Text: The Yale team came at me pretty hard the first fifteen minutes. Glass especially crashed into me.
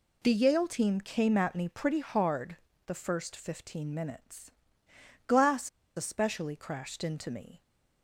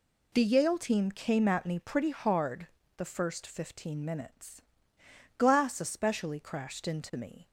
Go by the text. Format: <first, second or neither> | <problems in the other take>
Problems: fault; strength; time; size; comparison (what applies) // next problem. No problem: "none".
second | pauses between "hard" and "the"; slight; at 2.5 s; 0.32 s long; slight in the second // pauses between "Glass" and "especially"; slight; at 5.6 s; 0.27 s long